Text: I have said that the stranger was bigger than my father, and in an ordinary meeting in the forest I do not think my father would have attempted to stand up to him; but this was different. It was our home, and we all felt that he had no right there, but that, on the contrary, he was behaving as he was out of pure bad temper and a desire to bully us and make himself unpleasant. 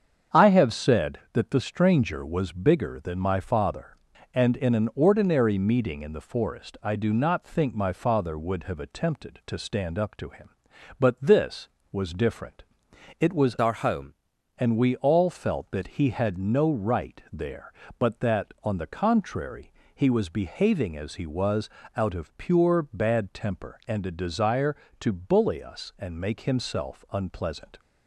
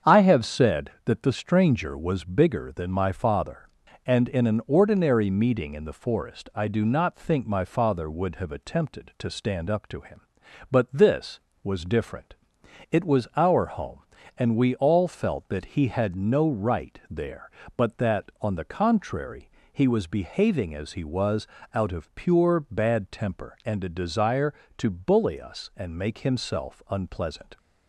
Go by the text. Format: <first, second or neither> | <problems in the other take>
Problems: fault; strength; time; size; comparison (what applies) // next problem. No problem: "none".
second | starts louder than the rest; strong; until 1.4 s; 7.5 dB; strong in the second // changes voice from "our" to "home"; from 13.6 to 14.1 s; 0.5 s long // pauses between "was" and "out"; slight; at 21.6 s; 0.28 s long; slight in the second